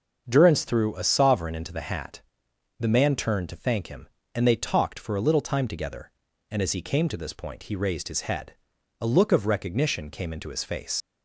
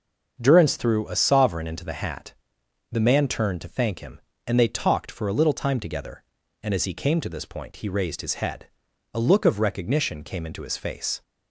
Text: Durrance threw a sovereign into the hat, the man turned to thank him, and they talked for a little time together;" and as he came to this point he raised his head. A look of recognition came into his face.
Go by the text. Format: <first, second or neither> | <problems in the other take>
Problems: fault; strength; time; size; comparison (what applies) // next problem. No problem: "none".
second | starts louder than the rest; until 1.2 s; 6.5 dB; also in the second // leaves "face" unfinished; at 11.0 s; 80 ms